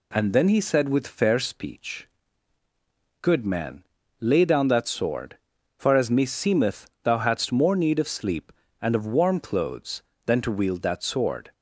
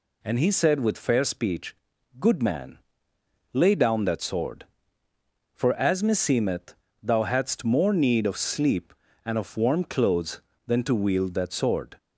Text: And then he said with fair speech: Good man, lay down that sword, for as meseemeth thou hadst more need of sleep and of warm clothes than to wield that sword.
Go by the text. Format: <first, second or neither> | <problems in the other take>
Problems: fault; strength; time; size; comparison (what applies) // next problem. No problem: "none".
first | skips "then"; at 0.3 s // pauses between "meseemeth" and "thou"; slight; at 6.7 s; 0.26 s long; slight in the first